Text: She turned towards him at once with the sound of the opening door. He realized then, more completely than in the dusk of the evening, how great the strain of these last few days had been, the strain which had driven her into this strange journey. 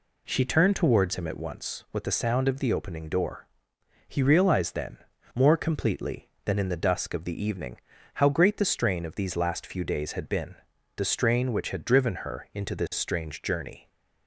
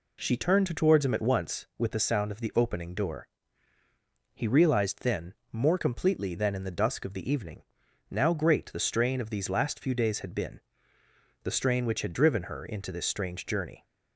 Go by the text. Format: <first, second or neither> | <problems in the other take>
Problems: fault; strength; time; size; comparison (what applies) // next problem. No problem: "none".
first | says "now" for "how"; at 8.0 s